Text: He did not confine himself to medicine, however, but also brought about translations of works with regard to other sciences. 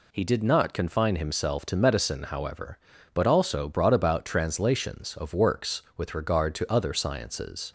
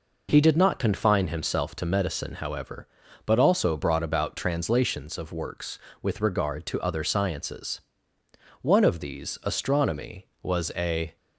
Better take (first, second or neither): first